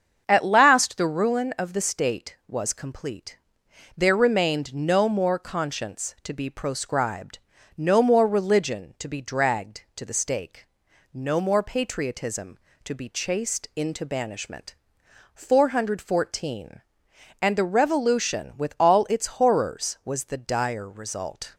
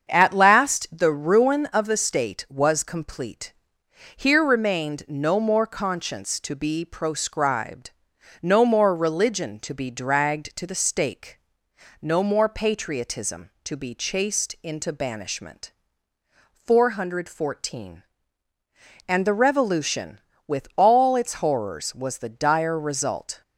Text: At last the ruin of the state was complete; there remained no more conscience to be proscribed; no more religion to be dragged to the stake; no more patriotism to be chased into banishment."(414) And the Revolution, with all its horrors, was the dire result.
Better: first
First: starts louder than the rest; until 1.2 s; 7 dB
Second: starts louder than the rest; strong; until 1.1 s; 7 dB // says "here" for "there"; at 4.1 s

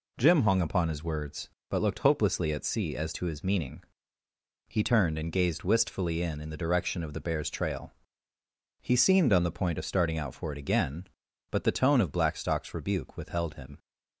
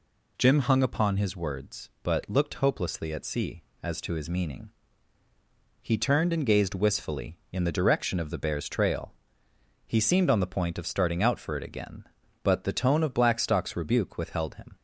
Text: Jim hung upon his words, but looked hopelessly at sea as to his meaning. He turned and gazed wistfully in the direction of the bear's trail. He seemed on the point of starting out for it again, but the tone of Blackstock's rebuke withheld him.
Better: second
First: says "in" twice; at 6.4 s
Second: none

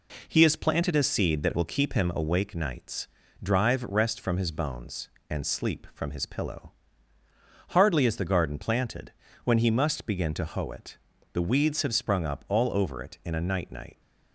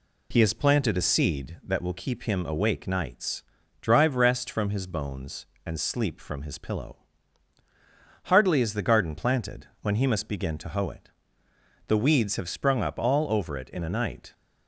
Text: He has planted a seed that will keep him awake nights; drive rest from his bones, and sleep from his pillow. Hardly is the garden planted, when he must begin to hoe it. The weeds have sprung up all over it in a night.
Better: second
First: says "night" twice; at 13.7 s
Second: none

